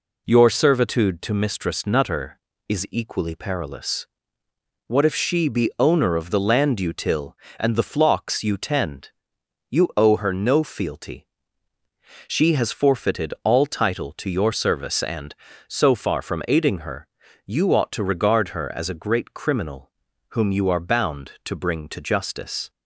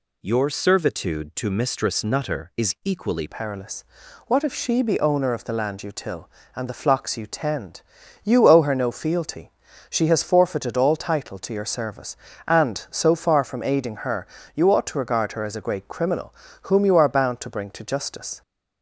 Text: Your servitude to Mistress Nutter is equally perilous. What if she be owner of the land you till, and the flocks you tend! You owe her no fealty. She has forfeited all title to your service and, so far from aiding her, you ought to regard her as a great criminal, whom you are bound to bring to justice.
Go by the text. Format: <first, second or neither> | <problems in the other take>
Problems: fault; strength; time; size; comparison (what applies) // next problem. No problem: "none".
first | changes voice at "perilous"; from 3.2 s on; 15.2 s long